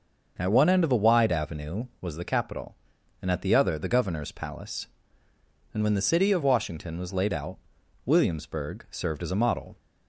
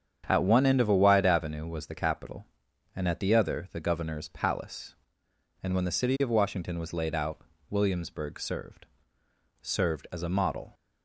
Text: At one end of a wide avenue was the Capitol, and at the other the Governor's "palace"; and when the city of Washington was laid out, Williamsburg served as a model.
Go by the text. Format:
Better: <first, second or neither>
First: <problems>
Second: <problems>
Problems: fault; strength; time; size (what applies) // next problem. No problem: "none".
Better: first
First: starts louder than the rest; until 1.3 s; 6.5 dB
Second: starts louder than the rest; strong; until 1.2 s; 8 dB // says "served" twice; at 9.6 s